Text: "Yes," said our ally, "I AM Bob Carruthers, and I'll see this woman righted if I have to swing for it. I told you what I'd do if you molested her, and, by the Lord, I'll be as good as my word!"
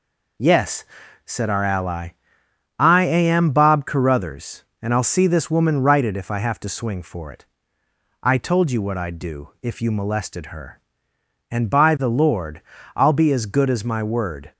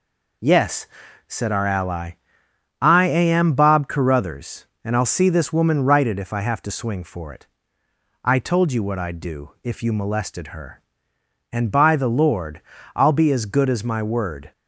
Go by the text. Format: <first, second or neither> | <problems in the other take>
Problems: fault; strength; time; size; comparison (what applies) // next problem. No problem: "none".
neither | none